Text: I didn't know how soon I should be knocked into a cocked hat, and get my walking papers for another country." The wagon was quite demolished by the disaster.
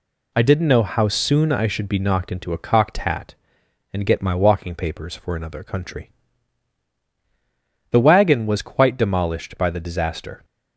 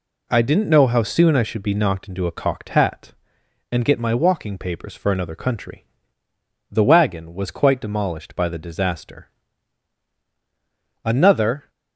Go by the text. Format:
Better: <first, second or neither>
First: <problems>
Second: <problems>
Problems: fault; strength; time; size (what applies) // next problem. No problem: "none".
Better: first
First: none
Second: goes on to say "Another"; noticeable; from 11.0 s on; 0.68 s long